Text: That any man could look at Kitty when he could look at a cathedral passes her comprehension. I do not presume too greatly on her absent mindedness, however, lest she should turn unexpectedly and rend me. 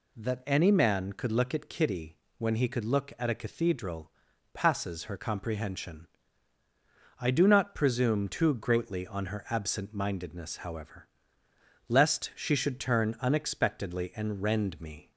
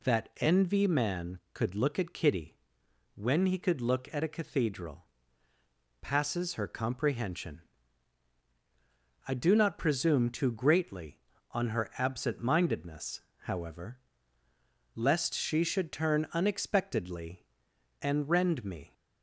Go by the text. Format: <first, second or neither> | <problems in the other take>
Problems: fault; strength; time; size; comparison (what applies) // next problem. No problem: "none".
first | says "envy" for "any"; at 0.3 s // pauses between "Kitty" and "when"; noticeable; at 2.5 s; 0.58 s long; slight in the first // pauses between "cathedral" and "passes"; noticeable; at 5.0 s; 0.96 s long; also in the first